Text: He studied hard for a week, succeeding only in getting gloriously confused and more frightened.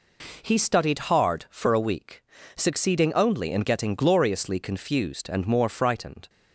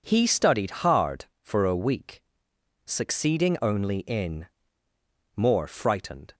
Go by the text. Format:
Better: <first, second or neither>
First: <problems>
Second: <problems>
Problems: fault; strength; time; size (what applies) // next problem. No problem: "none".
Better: first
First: none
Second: skips "getting gloriously confused and"; at 4.8 s